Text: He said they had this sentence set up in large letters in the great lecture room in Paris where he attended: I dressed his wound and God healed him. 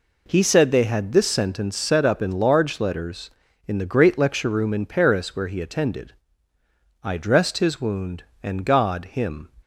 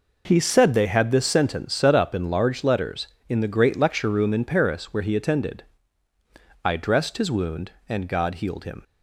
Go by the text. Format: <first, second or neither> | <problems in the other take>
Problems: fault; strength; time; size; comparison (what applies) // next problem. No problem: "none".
second | skips "healed"; at 9.0 s